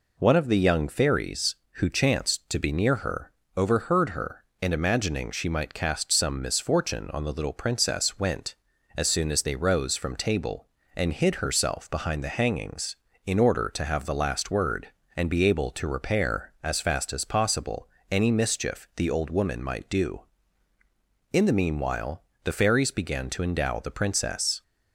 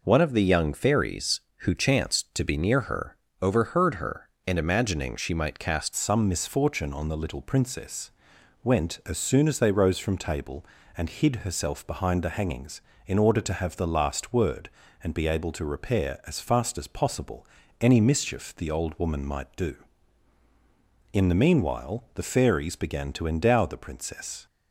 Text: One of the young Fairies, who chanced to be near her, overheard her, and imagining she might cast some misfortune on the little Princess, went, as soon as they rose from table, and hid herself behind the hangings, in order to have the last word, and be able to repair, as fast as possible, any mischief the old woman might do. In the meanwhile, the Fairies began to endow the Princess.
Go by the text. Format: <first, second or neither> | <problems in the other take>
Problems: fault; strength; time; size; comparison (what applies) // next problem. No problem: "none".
first | changes voice at "some"; from 5.9 s on; 18.5 s long